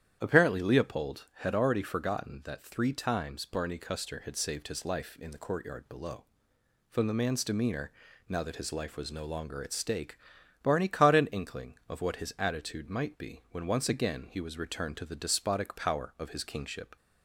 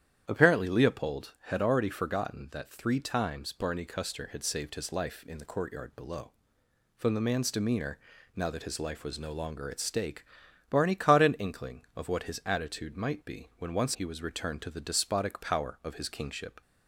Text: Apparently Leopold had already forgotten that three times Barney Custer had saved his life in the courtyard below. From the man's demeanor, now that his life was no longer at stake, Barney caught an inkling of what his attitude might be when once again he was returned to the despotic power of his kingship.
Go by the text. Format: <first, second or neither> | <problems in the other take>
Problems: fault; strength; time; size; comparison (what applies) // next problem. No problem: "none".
first | starts louder than the rest; strong; until 1.2 s; 10 dB; strong in the first // skips "again"; at 13.9 s